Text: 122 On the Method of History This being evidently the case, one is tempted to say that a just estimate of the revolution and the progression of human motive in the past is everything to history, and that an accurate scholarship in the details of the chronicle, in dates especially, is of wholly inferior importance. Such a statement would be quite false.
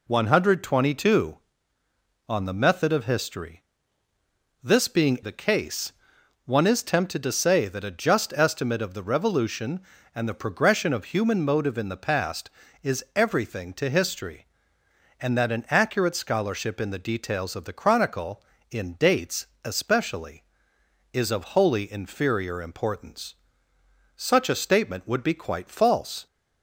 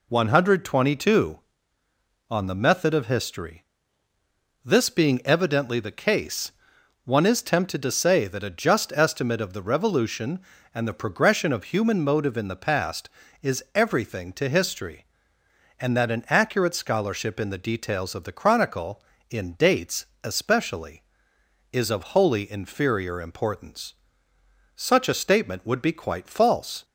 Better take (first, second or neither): second